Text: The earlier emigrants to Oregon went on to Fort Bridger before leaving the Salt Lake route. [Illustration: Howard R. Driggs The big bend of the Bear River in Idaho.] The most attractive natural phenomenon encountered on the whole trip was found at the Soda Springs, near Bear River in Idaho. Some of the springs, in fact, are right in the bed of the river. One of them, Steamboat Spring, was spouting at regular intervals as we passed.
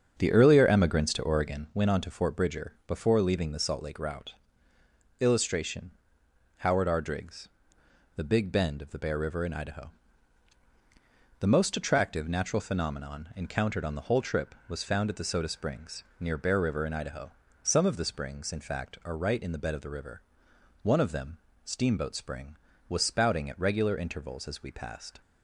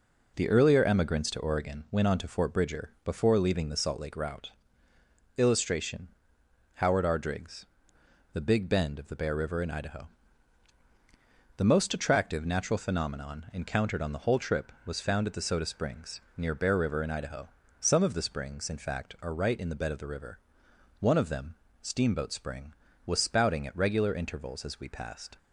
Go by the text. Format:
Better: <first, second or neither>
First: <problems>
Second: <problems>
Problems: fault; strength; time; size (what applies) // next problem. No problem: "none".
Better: second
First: starts louder than the rest; until 1.8 s; 7 dB // pauses between "Driggs" and "The"; noticeable; at 7.4 s; 0.66 s long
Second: pauses between "Driggs" and "The"; noticeable; at 7.6 s; 0.66 s long